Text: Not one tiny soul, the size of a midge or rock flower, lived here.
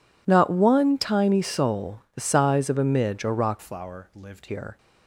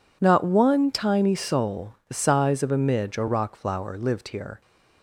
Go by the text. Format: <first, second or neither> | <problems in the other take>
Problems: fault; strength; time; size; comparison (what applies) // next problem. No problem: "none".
second | changes voice from "flower" to "lived"; from 3.6 to 4.4 s; 0.8 s long